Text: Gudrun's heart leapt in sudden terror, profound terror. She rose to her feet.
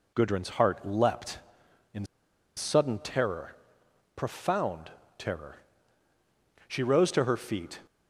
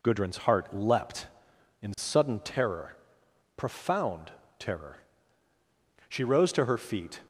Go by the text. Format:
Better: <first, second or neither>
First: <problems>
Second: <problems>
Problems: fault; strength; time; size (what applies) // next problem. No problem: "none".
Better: second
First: pauses between "in" and "sudden"; noticeable; at 2.0 s; 0.51 s long // pauses between "profound" and "terror"; slight; at 4.9 s; 0.26 s long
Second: pauses between "profound" and "terror"; slight; at 4.3 s; 0.26 s long